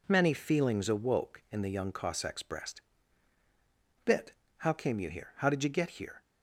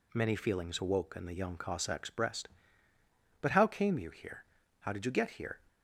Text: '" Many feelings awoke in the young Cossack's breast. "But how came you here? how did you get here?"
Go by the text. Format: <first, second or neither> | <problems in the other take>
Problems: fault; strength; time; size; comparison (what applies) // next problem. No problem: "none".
second | says "Bit" for "But"; at 4.0 s